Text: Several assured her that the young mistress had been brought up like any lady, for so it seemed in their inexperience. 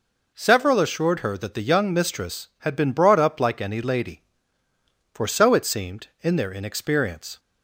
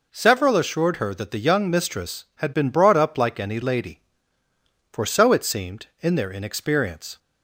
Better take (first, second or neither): neither